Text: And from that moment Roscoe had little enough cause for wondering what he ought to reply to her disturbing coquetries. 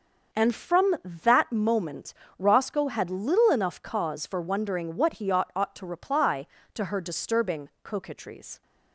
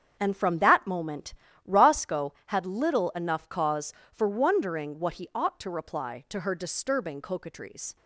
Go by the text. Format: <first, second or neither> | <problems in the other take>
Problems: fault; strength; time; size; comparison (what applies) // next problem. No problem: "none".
second | starts louder than the rest; until 1.4 s; 6.5 dB; strong in the second // pauses between "moment" and "Roscoe"; slight; at 2.1 s; 0.24 s long; slight in the second // says "ought" twice; at 5.5 s // pauses between "disturbing" and "coquetries"; slight; at 7.6 s; 0.16 s long